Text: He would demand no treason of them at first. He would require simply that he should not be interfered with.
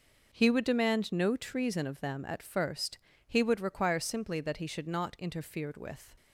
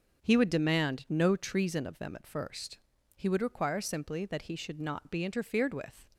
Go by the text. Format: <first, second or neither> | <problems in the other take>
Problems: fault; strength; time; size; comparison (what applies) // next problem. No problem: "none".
second | skips "be"; at 5.1 s